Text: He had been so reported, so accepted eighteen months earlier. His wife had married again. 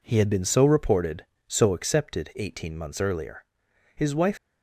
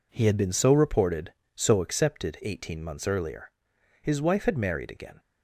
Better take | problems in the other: second | stops before "had married again"; at 4.3 s

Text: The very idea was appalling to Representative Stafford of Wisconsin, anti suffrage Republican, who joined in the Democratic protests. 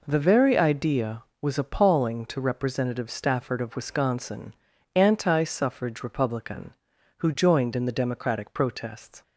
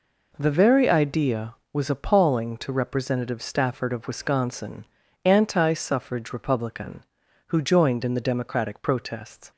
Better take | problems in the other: neither | none

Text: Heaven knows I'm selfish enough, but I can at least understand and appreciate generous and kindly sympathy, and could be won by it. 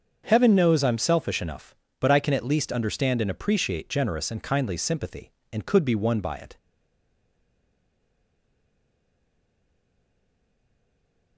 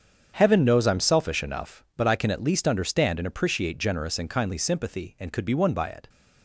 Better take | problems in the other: second | starts louder than the rest; until 1.2 s; 7 dB; strong in the second // stays silent after the last word; strong; from 6.5 s on; 4.8 s long

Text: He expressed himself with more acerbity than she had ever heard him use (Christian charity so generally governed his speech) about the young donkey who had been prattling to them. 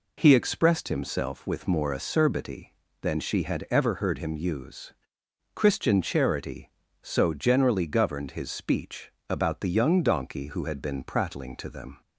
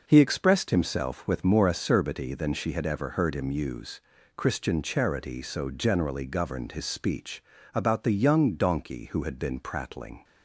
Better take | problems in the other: first | stops before "to them"; at 10.2 s

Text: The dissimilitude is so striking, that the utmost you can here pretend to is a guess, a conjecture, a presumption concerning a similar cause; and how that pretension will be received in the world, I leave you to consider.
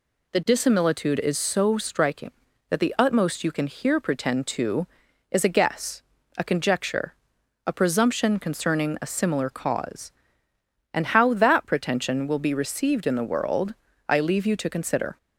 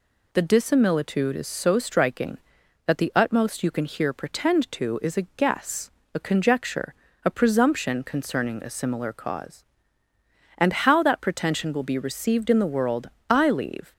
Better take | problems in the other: first | stops before "you to consider"; at 13.9 s

